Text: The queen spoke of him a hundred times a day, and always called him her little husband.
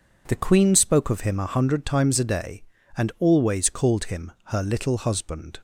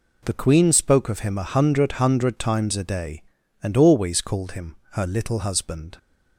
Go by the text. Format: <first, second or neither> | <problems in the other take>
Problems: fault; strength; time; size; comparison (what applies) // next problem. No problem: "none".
first | says "hundred" twice; at 1.9 s // pauses between "him" and "her"; slight; at 4.7 s; 0.16 s long